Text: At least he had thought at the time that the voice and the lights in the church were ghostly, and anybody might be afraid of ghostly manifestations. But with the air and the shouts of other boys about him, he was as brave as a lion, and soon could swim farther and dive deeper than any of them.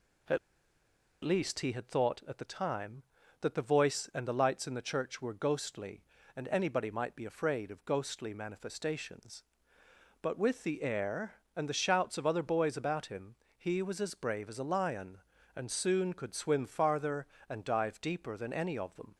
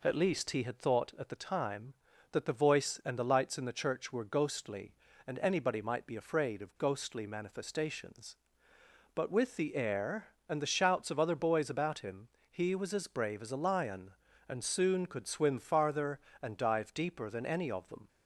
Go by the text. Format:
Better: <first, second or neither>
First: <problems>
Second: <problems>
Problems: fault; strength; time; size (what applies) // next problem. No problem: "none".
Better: second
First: pauses between "At" and "least"; noticeable; at 0.3 s; 0.86 s long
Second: none